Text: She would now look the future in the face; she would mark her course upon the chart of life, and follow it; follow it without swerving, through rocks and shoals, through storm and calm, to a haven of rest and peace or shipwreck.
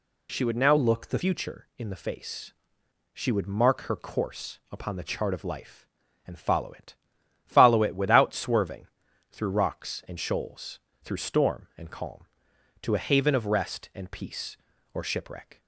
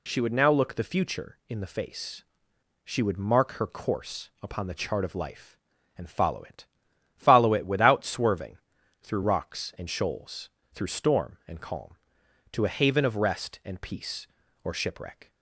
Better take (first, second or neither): second